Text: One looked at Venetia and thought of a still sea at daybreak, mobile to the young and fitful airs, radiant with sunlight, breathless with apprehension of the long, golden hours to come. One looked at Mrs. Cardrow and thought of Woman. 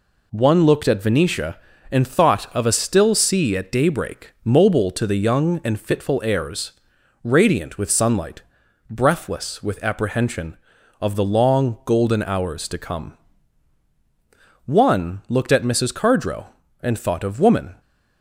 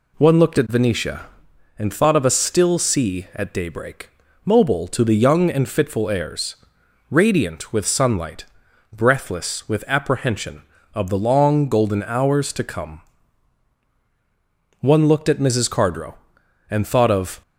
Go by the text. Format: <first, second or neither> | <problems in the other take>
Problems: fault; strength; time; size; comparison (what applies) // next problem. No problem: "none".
first | stops before "Woman"; at 17.4 s